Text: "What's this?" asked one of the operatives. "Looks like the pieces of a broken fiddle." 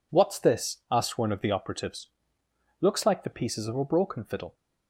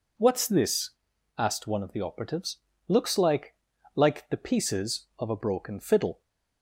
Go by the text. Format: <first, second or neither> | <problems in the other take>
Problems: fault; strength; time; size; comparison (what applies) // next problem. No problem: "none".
first | says "like" twice; at 3.9 s